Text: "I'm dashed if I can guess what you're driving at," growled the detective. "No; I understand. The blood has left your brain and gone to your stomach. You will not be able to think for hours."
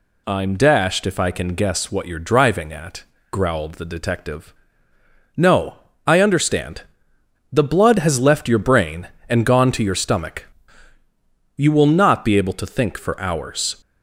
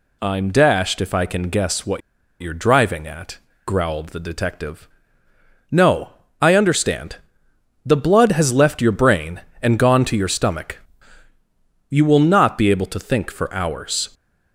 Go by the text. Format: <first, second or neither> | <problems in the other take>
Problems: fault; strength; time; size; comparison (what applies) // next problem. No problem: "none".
first | pauses between "what" and "you're"; at 2.0 s; 0.39 s long